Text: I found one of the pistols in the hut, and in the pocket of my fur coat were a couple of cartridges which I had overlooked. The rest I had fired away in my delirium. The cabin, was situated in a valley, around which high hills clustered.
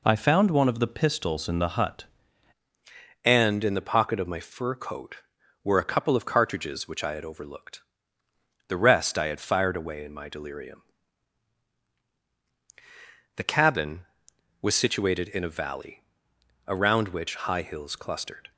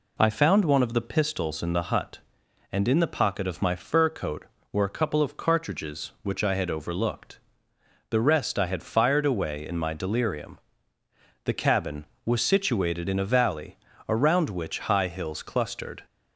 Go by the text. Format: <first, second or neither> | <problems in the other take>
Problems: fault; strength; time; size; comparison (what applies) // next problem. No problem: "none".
second | changes voice at "and"; from 3.2 s on; 15.3 s long